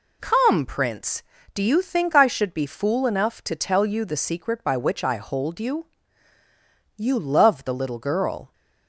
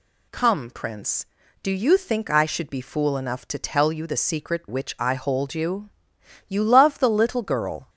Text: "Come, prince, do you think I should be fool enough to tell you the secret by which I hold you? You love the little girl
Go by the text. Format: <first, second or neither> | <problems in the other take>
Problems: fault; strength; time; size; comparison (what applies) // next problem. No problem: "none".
first | skips "by"; at 4.6 s